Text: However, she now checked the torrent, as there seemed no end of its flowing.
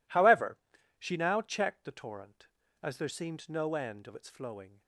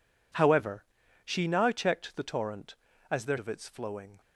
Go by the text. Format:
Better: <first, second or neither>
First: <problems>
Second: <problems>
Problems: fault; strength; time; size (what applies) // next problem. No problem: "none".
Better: first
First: none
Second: skips "seemed no end"; at 3.3 s